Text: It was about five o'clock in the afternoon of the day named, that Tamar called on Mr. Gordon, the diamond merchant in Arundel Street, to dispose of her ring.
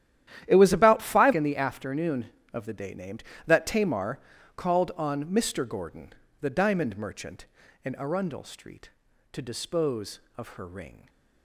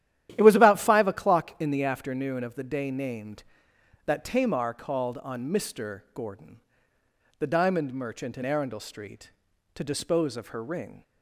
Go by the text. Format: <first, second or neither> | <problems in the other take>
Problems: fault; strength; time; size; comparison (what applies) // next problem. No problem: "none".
second | starts louder than the rest; strong; until 1.4 s; 11.5 dB; strong in the second // skips "o'clock"; at 1.3 s // pauses between "Tamar" and "called"; slight; at 4.1 s; 0.36 s long